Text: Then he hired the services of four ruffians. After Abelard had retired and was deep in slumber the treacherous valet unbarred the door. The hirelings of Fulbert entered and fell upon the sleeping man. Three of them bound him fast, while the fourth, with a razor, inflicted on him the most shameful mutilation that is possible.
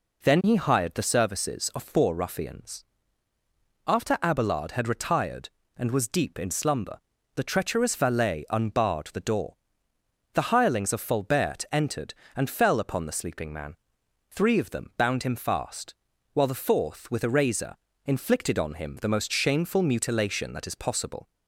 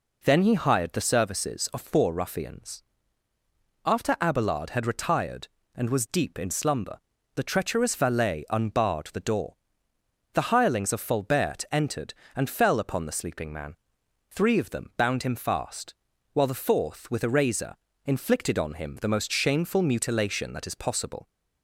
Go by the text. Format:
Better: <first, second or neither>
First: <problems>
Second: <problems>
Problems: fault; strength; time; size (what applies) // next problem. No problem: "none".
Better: neither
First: pauses between "slumber" and "the"; at 6.9 s; 0.38 s long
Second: pauses between "slumber" and "the"; at 6.9 s; 0.38 s long